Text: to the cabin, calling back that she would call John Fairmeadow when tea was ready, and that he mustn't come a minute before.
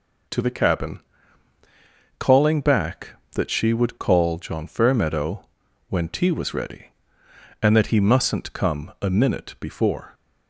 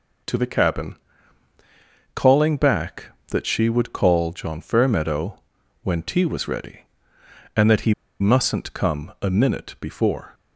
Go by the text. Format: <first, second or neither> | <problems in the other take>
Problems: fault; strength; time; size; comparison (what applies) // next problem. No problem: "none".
first | pauses between "Fairmeadow" and "when"; at 5.3 s; 0.42 s long; also in the first // pauses between "he" and "mustn't"; slight; at 7.9 s; 0.26 s long